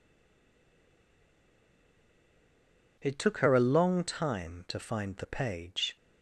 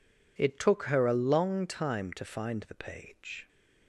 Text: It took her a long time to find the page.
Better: second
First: stays silent before the first word; strong; until 2.9 s; 2.9 s long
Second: none

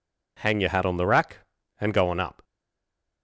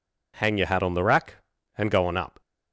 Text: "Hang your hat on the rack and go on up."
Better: second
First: stays silent after the last word; slight; from 2.4 s on; 0.8 s long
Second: none

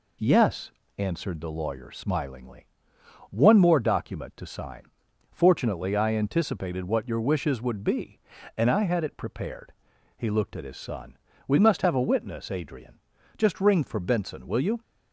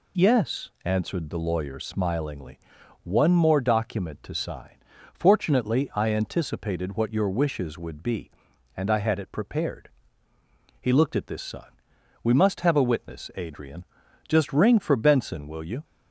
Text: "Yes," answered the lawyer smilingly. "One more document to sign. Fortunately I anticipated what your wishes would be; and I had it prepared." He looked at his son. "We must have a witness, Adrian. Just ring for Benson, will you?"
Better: first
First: none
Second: says "this" for "his"; at 11.2 s

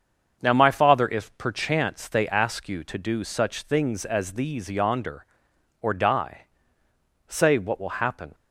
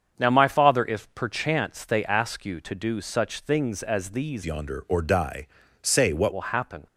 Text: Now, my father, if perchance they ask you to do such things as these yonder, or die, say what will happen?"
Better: first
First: starts louder than the rest; until 1.4 s; 7 dB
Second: starts louder than the rest; strong; until 1.1 s; 7 dB // changes voice from "yonder" to "what"; from 4.4 to 6.3 s; 1.9 s long

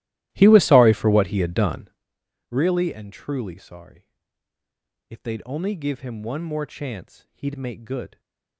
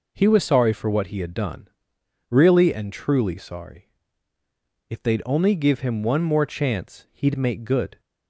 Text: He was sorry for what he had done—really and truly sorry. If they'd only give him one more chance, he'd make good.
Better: second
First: starts louder than the rest; strong; until 2.0 s; 15.5 dB // stays silent after the last word; slight; from 8.0 s on; 0.5 s long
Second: none

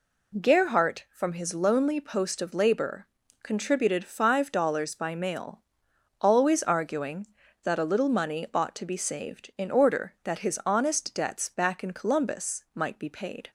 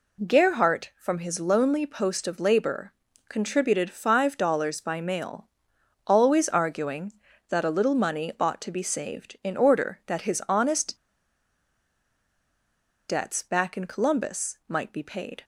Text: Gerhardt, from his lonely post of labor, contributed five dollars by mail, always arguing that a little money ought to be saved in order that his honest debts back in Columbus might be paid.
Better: first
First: none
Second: pauses between "honest" and "debts"; strong; at 10.9 s; 2.1 s long

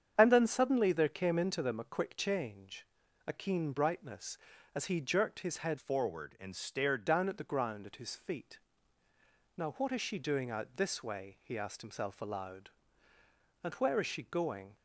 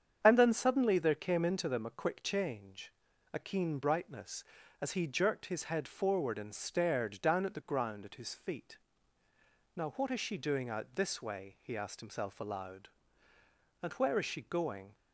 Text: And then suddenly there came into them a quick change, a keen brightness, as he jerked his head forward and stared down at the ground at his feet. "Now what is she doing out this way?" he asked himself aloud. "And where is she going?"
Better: second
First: starts louder than the rest; strong; until 1.1 s; 8 dB // changes voice from "forward" to "stared"; from 5.7 to 7.0 s; 1.3 s long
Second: starts louder than the rest; strong; until 1.2 s; 8 dB

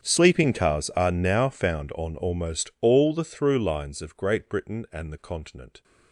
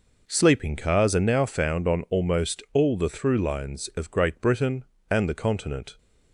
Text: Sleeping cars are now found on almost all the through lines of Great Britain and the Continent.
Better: second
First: gets quieter; strong; throughout; 24 dB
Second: none

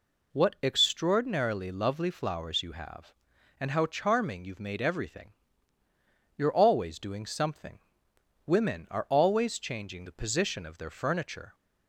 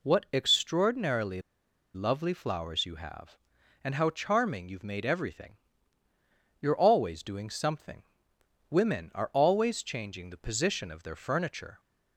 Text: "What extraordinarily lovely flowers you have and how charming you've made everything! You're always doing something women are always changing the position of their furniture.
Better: first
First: pauses between "something" and "women"; noticeable; at 7.7 s; 0.66 s long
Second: pauses between "extraordinarily" and "lovely"; noticeable; at 1.4 s; 0.54 s long // pauses between "something" and "women"; noticeable; at 8.0 s; 0.66 s long

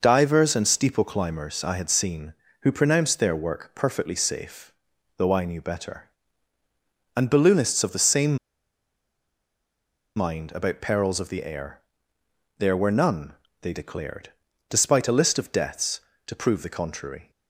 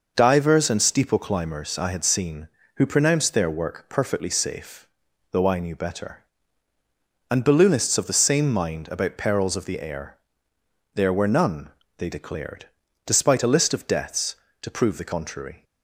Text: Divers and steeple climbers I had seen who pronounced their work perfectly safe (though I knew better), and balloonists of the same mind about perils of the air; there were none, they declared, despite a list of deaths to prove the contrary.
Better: second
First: pauses between "same" and "mind"; strong; at 8.3 s; 1.7 s long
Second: none

